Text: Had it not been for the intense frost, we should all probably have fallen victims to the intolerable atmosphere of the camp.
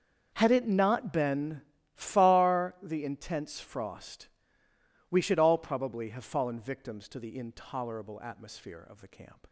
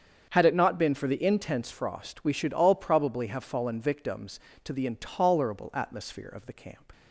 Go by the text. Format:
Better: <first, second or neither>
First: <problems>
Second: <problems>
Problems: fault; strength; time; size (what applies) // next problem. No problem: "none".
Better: second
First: starts louder than the rest; until 1.3 s; 6.5 dB // says "far" for "for"; at 1.9 s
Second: starts louder than the rest; strong; until 1.3 s; 7.5 dB